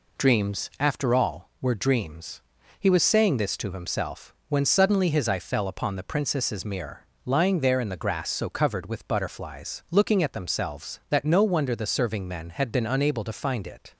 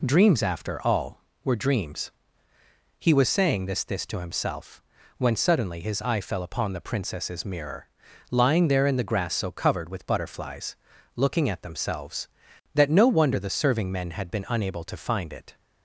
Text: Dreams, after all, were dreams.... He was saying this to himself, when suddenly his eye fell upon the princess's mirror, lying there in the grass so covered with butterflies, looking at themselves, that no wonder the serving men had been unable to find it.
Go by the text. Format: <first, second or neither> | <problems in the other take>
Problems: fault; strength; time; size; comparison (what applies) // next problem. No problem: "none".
first | says "this" twice; at 3.8 s